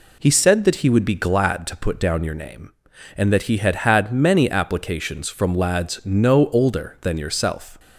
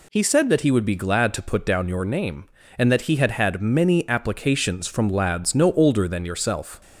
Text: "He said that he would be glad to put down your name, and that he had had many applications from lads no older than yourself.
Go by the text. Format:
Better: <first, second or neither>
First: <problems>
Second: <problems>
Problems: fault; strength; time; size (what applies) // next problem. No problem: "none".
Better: neither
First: none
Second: none